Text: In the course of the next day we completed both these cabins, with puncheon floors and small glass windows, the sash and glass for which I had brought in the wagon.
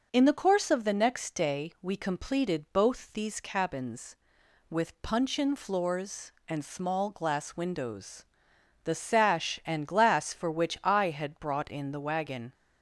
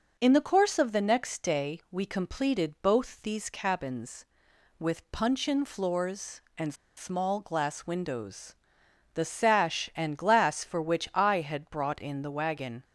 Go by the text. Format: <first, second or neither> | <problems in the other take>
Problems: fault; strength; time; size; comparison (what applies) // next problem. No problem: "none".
first | pauses between "and" and "small"; slight; at 6.7 s; 0.23 s long